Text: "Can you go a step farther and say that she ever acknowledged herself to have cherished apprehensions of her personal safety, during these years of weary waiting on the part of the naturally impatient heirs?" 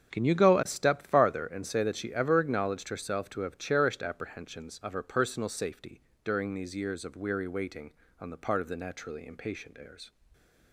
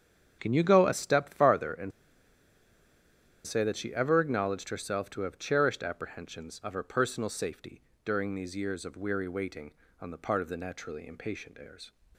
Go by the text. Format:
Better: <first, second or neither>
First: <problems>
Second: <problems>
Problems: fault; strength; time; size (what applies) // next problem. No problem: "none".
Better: first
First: starts louder than the rest; strong; until 1.1 s; 7.5 dB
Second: starts louder than the rest; strong; until 1.4 s; 7.5 dB // pauses between "and" and "say"; strong; at 1.9 s; 1.5 s long